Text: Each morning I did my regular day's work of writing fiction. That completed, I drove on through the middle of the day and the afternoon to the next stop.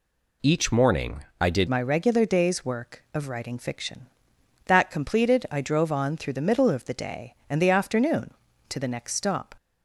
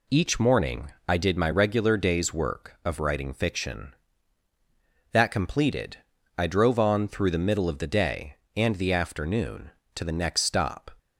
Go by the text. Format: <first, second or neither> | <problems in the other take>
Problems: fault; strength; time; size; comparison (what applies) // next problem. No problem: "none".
second | changes voice at "my"; from 1.6 s on; 7.9 s long